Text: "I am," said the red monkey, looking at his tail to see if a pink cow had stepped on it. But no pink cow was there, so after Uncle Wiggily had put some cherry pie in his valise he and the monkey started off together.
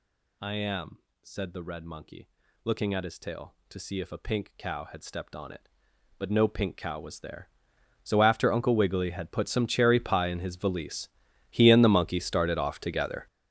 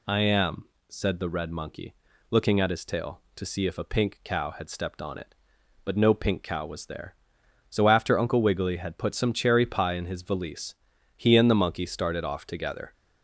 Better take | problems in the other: second | gets louder; strong; throughout; 13 dB // pauses between "valise" and "he"; at 11.0 s; 0.40 s long; also in the second

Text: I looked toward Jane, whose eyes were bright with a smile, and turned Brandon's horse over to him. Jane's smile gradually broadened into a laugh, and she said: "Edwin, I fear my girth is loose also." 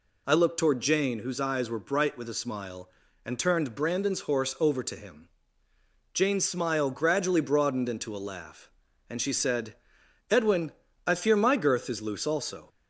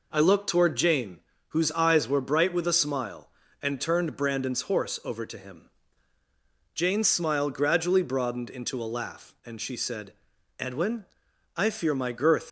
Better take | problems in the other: first | stops before "is loose also"; at 12.4 s

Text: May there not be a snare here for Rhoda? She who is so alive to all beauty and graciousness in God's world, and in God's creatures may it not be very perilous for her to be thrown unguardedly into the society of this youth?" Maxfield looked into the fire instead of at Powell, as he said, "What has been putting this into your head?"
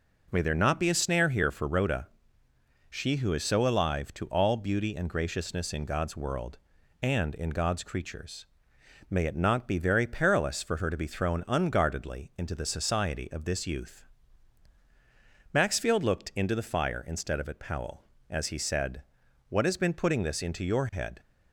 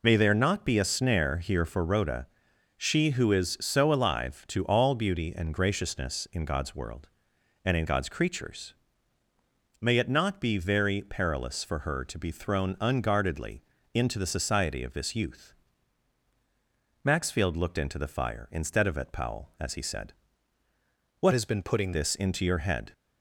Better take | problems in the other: first | pauses between "creatures" and "may"; at 8.7 s; 1.0 s long; noticeable in the first // pauses between "unguardedly" and "into"; slight; at 13.6 s; 0.32 s long // changes voice from "has" to "putting"; from 21.3 to 21.9 s; 0.6 s long

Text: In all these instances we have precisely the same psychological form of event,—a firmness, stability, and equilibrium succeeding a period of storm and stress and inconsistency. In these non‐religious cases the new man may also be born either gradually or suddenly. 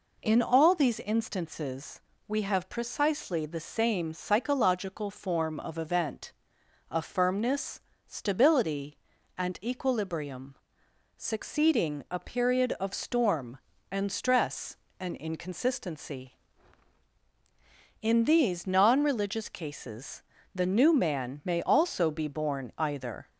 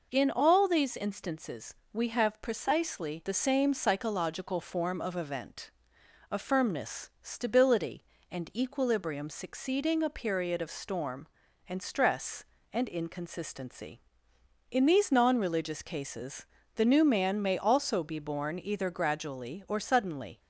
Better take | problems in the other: second | pauses between "instances" and "we"; slight; at 2.0 s; 0.26 s long; slight in the second // pauses between "equilibrium" and "succeeding"; noticeable; at 10.5 s; 0.60 s long // pauses between "cases" and "the"; slight; at 20.2 s; 0.32 s long; slight in the second // stops before "gradually or suddenly"; at 23.2 s

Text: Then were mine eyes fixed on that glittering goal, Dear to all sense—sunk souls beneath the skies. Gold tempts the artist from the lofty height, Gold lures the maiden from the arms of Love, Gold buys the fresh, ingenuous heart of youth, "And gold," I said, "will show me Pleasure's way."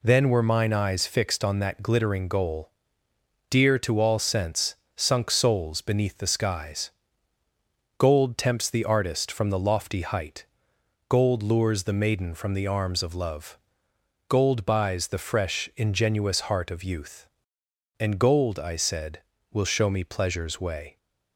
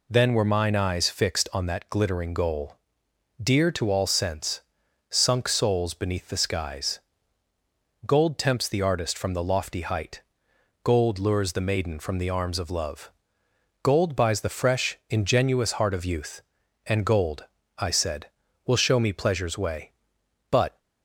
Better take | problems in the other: first | goes on to say "But"; slight; from 20.4 s on; 0.28 s long

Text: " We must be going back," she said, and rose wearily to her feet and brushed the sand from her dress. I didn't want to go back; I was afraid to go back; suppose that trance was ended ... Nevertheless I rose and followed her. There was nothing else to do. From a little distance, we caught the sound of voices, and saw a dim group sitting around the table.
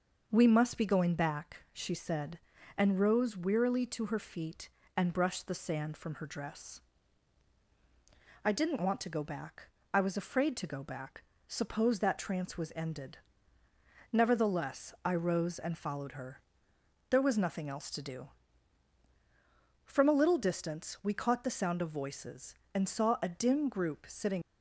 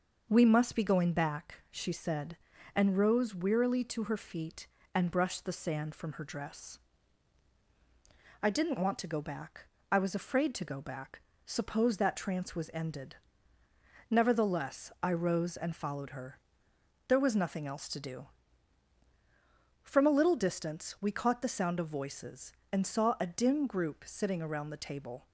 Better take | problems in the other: second | stops before "around the table"; at 24.4 s

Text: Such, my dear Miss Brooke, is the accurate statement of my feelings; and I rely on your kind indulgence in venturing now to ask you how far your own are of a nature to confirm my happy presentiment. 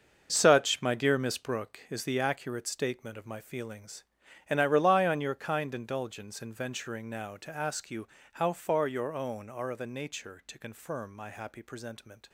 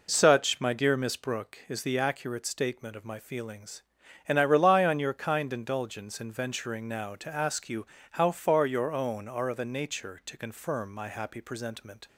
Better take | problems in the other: second | gets quieter; strong; throughout; 10.5 dB // pauses between "you" and "how"; slight; at 8.0 s; 0.28 s long; slight in the second

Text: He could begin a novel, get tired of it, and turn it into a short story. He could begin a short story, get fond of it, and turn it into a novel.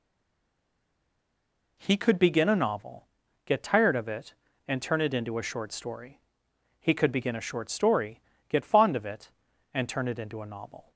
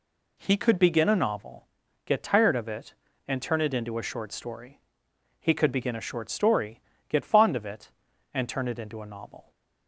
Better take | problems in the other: second | stays silent before the first word; noticeable; until 1.7 s; 1.7 s long

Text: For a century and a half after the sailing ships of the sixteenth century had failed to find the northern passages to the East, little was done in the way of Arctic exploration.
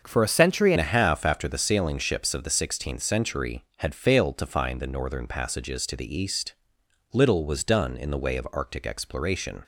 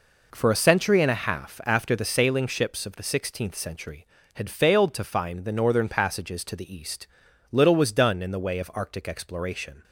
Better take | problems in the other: second | starts louder than the rest; until 1.0 s; 6.5 dB // changes voice at "and"; from 0.7 s on; 8.9 s long

